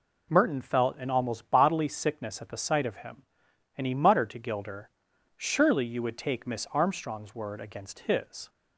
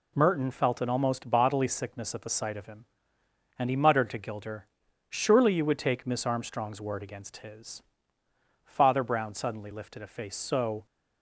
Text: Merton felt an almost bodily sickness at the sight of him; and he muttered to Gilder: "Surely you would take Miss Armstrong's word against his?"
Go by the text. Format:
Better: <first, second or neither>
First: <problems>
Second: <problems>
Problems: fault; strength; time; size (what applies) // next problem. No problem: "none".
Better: first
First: none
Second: goes on to say "Father Brown suddenly lifted a face so"; strong; from 8.6 s on; 2.2 s long